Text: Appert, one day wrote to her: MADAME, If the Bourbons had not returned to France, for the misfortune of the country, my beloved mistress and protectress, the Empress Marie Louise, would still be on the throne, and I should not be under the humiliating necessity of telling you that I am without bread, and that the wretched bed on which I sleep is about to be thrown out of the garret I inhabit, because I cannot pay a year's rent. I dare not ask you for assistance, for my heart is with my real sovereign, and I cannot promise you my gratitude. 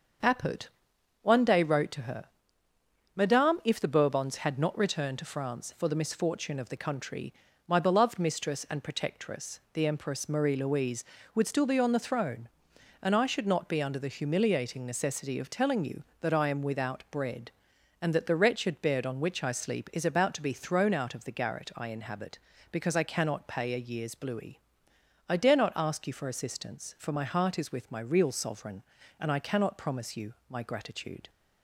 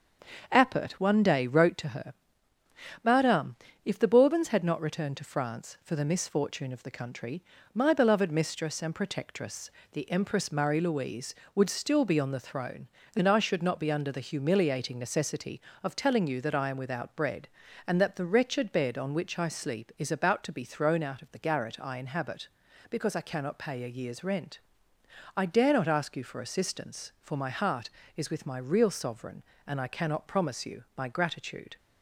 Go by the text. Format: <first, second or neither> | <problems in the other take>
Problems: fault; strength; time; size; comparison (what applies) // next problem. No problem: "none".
second | starts louder than the rest; until 1.8 s; 6.5 dB; also in the second // says "bluey" for "rent"; at 24.1 s // pauses between "you" and "my"; slight; at 30.3 s; 0.16 s long